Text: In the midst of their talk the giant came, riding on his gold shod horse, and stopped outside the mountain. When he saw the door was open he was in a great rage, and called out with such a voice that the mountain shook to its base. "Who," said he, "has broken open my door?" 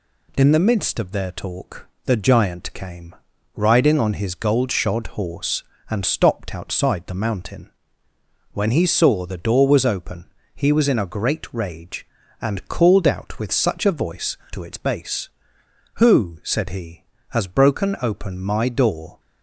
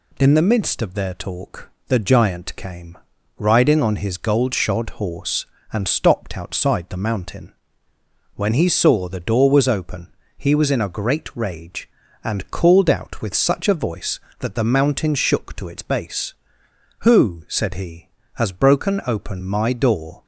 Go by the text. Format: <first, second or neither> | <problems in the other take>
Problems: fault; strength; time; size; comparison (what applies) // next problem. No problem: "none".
second | pauses between "talk" and "the"; slight; at 1.8 s; 0.18 s long; slight in the second // pauses between "open" and "he"; slight; at 10.2 s; 0.24 s long; slight in the second // skips "that the mountain shook"; at 14.4 s